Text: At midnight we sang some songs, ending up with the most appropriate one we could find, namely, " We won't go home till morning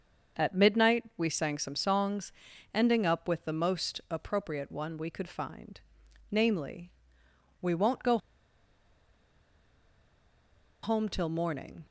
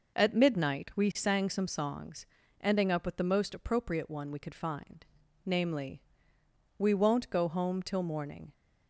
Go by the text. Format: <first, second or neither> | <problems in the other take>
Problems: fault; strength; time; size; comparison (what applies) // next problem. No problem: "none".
second | starts louder than the rest; until 1.5 s; 7 dB // pauses between "go" and "home"; strong; at 8.1 s; 2.6 s long